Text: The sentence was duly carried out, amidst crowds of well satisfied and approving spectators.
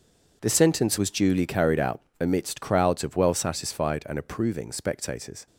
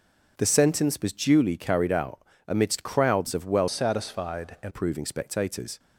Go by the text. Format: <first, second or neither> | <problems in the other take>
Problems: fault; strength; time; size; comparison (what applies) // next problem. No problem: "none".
first | starts louder than the rest; until 1.3 s; 6 dB // changes voice from "satisfied" to "and"; from 3.6 to 4.7 s; 1.1 s long